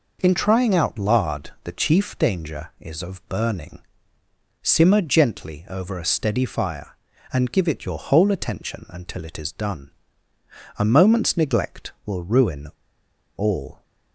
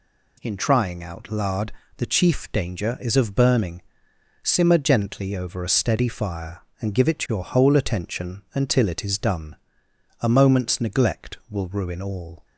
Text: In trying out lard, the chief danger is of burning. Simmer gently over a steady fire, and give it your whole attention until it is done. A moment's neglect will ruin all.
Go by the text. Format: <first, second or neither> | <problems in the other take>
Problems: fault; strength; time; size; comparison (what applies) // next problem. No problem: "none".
second | pauses between "ruin" and "all"; noticeable; at 12.6 s; 0.70 s long